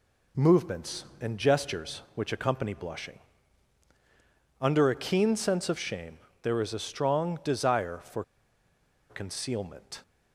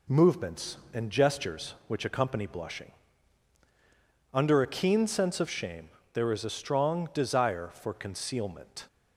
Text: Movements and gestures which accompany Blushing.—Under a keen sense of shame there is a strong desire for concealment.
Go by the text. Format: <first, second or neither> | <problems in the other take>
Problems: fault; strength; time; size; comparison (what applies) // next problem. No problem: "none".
second | pauses between "shame" and "there"; slight; at 6.1 s; 0.24 s long; slight in the second // pauses between "for" and "concealment"; noticeable; at 8.2 s; 0.87 s long